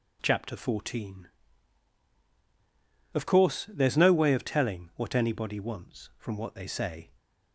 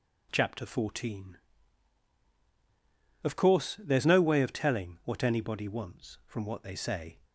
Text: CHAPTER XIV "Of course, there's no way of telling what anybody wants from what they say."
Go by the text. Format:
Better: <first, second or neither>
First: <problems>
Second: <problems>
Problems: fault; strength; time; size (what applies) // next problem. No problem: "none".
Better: neither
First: none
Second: none